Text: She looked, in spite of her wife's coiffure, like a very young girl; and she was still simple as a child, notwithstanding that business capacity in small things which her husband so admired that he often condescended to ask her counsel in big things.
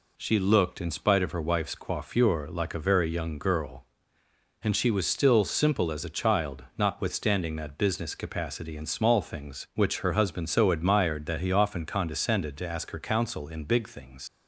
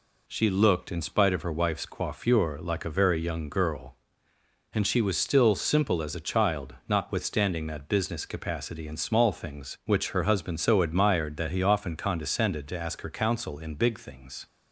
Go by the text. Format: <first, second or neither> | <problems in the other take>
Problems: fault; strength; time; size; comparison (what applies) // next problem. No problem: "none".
second | leaves "things" unfinished; at 14.2 s; 80 ms